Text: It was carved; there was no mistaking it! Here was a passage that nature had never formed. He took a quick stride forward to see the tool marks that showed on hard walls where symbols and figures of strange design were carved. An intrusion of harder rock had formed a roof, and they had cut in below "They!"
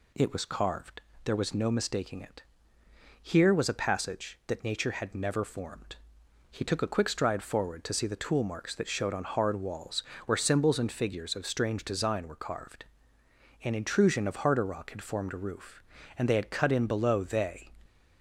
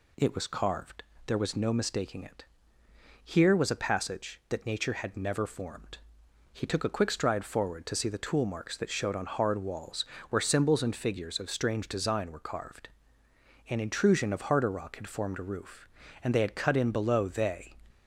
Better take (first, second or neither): neither